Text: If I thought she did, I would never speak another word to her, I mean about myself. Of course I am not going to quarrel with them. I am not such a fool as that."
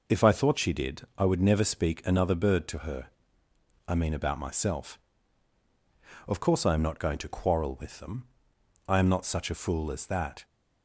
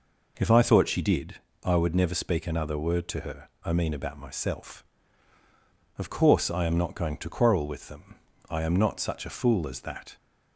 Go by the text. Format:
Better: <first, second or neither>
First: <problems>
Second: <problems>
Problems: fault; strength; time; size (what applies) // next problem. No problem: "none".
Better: second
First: says "bird" for "word"; at 2.3 s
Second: none